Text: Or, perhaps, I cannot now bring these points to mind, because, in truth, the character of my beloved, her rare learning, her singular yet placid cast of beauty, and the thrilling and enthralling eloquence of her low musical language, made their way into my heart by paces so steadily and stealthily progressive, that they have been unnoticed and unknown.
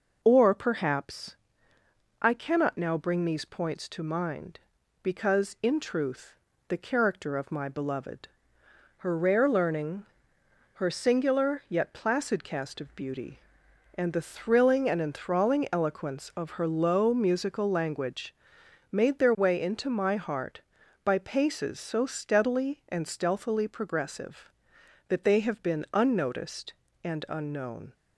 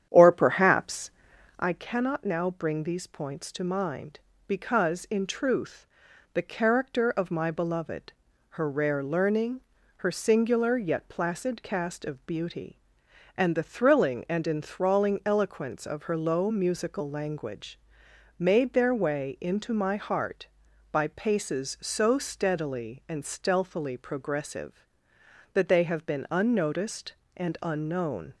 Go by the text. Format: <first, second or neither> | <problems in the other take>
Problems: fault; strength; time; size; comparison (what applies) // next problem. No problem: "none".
first | starts louder than the rest; strong; until 1.8 s; 9.5 dB